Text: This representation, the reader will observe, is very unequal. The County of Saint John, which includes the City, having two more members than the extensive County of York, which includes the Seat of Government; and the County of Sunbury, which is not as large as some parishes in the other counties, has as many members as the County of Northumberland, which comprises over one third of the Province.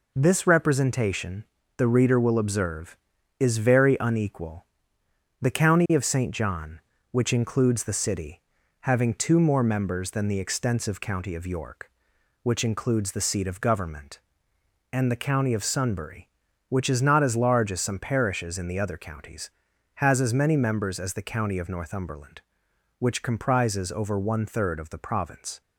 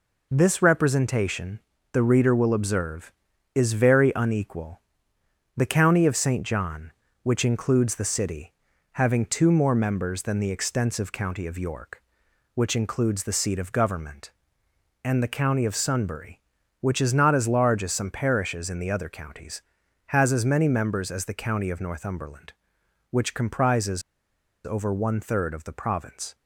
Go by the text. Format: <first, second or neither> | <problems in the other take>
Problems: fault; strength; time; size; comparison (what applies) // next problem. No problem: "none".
first | pauses between "comprises" and "over"; noticeable; at 24.0 s; 0.63 s long